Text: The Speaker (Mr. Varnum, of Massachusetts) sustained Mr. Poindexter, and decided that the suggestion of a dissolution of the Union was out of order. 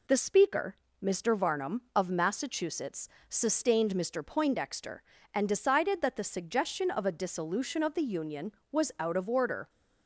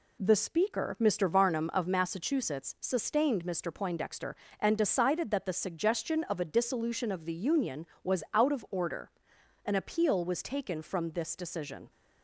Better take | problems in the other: first | goes on to say "An appeal was taken from this decision"; strong; from 9.6 s on; 2.2 s long

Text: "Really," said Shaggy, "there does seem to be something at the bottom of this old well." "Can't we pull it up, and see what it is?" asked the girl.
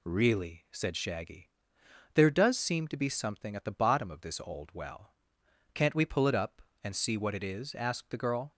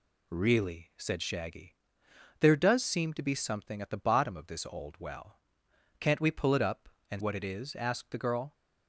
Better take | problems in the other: first | skips "see"; at 7.2 s

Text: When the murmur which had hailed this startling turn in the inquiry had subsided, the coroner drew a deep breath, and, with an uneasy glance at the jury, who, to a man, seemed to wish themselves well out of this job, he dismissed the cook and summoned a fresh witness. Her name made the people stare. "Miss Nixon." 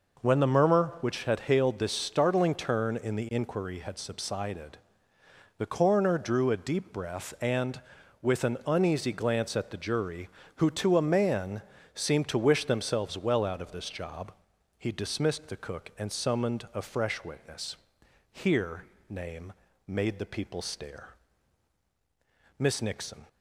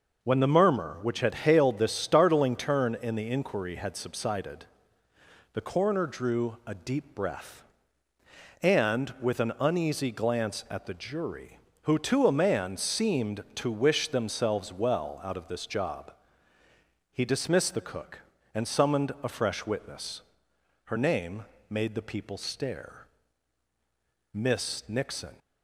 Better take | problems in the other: second | says "Here" for "Her"; at 18.3 s // pauses between "name" and "made"; slight; at 19.5 s; 0.36 s long; slight in the second

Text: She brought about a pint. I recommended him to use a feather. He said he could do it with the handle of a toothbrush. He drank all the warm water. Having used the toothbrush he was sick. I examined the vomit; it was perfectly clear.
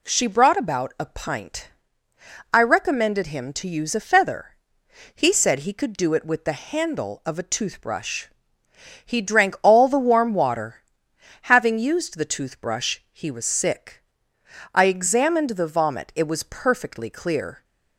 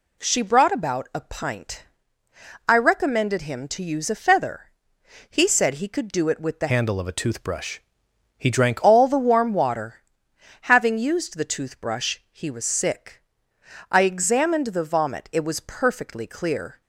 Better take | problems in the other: first | changes voice from "handle" to "drank"; from 6.6 to 8.8 s; 2.2 s long

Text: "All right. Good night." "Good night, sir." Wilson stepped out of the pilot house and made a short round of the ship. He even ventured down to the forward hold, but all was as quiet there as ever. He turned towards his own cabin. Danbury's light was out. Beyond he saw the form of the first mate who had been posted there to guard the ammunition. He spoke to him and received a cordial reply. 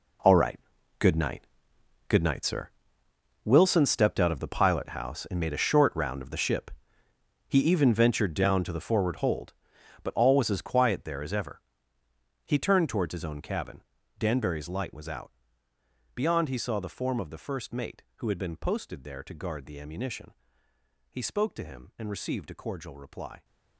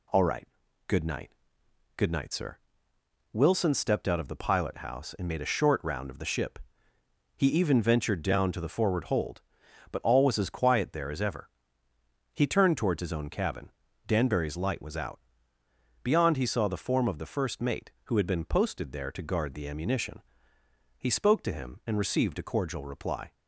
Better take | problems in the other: second | gets quieter; strong; throughout; 14 dB

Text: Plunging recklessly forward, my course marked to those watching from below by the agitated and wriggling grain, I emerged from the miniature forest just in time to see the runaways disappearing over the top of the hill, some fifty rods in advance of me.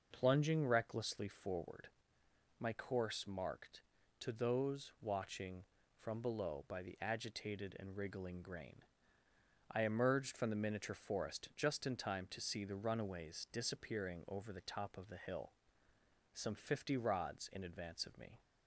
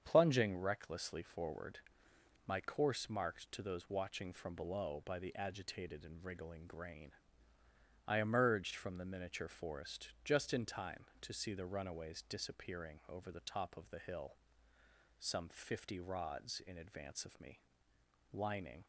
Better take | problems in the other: first | starts louder than the rest; strong; until 1.0 s; 7.5 dB // pauses between "forest" and "just"; slight; at 10.0 s; 0.16 s long // goes on to say "Lining"; from 18.3 s on; 0.52 s long

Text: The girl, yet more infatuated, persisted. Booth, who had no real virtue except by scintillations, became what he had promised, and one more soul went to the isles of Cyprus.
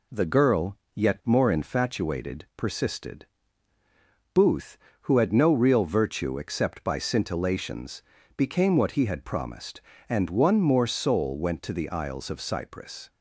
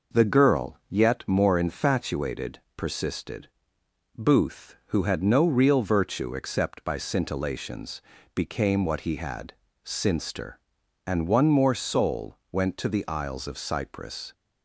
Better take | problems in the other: first | says "sinster" for "promised"; at 9.8 s

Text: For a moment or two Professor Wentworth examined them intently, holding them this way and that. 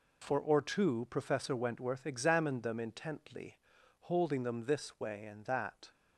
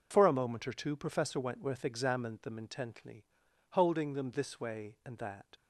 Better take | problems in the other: second | skips "a moment"; at 0.3 s

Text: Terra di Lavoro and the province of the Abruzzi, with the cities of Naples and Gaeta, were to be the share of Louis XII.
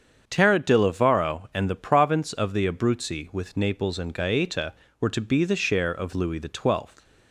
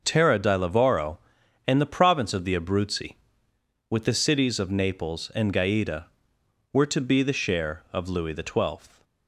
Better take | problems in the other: second | starts louder than the rest; strong; until 1.2 s; 7.5 dB; noticeable in the second // skips "the cities of"; at 3.5 s

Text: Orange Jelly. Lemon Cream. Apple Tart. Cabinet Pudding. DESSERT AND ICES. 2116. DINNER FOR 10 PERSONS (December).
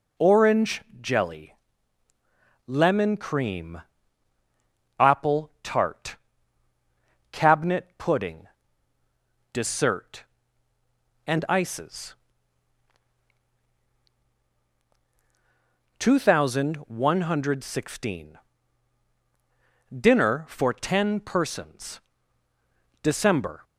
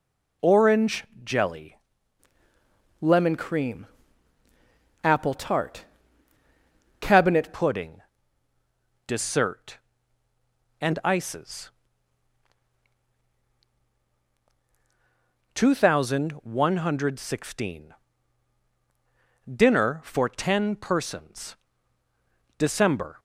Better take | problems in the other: first | pauses between "Orange" and "Jelly"; slight; at 1.0 s; 0.20 s long; slight in the first // changes voice from "Lemon" to "Cabinet"; from 3.0 to 7.5 s; 4.5 s long

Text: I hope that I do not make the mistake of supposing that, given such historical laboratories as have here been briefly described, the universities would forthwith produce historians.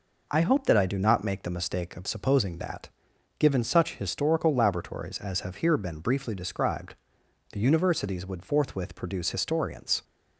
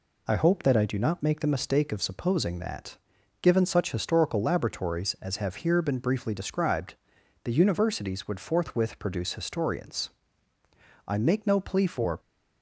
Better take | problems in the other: first | goes on to say "I make no plea for"; noticeable; from 11.0 s on; 1.1 s long

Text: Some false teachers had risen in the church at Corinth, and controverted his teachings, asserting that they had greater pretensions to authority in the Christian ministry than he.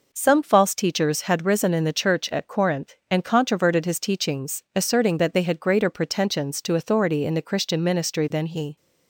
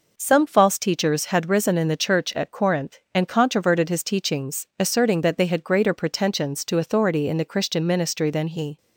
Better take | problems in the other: neither | none

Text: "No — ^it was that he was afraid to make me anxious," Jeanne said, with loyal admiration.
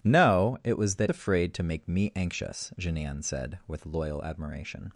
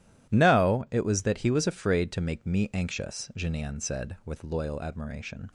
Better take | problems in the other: second | skips "he was"; at 1.0 s

